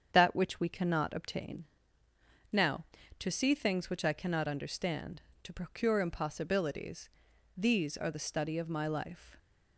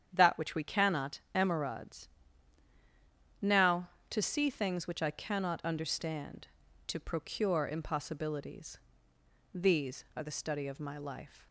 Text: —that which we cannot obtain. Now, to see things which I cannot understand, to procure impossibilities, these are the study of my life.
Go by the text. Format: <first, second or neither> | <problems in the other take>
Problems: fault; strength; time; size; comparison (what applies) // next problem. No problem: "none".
first | starts louder than the rest; strong; until 1.1 s; 9 dB; strong in the first // says "emerods" for "obtain"; at 1.3 s